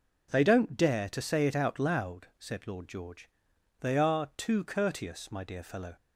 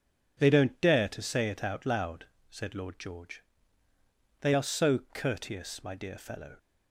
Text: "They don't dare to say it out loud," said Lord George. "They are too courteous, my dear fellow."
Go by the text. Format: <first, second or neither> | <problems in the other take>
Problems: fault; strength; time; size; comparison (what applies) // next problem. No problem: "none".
first | says "so" for "too"; at 4.6 s